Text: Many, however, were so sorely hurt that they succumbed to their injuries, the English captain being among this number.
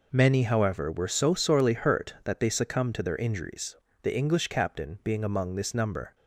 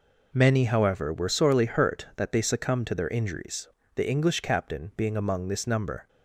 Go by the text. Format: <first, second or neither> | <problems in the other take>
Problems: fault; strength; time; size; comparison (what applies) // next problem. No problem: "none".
first | skips "so"; at 1.2 s